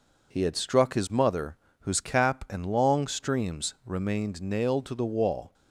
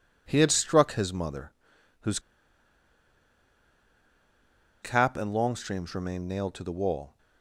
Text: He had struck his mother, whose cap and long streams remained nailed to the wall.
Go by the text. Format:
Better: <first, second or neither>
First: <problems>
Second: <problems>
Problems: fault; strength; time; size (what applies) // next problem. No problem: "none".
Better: first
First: none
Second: pauses between "whose" and "cap"; strong; at 2.1 s; 2.6 s long